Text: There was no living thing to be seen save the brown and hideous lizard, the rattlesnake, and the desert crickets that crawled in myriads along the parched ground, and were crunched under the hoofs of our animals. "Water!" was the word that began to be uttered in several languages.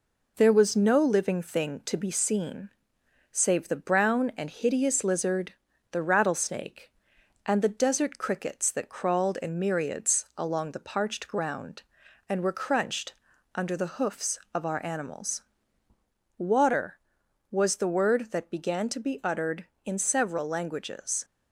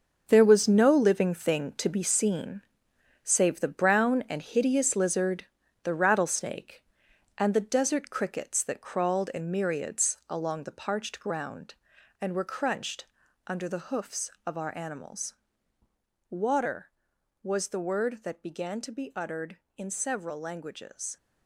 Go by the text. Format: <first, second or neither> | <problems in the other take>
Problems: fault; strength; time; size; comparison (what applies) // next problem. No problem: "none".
first | gets quieter; strong; throughout; 10 dB // pauses between "seen" and "save"; noticeable; at 2.6 s; 0.60 s long; noticeable in the first // pauses between "crunched" and "under"; at 13.0 s; 0.40 s long; also in the first